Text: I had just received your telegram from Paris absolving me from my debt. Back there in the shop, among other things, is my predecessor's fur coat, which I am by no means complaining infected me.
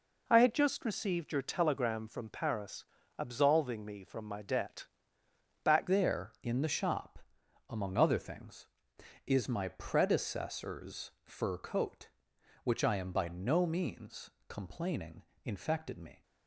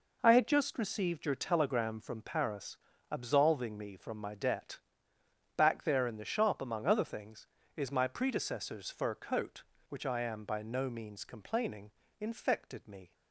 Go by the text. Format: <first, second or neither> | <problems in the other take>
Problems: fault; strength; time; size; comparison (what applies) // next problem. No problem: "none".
second | pauses between "Paris" and "absolving"; slight; at 2.8 s; 0.34 s long; slight in the second // changes voice at "there"; from 5.8 s on; 10.4 s long // pauses between "means" and "complaining"; slight; at 14.3 s; 0.18 s long // pauses between "complaining" and "infected"; slight; at 15.2 s; 0.22 s long; slight in the second